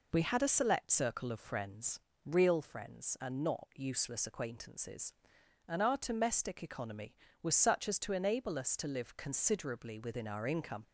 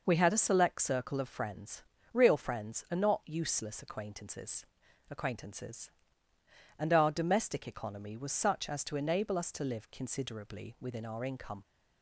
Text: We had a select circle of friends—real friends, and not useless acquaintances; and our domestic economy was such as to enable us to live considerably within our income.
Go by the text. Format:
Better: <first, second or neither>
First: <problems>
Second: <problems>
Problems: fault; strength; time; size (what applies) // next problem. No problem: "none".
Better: first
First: none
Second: says "acquaintances" twice; at 5.0 s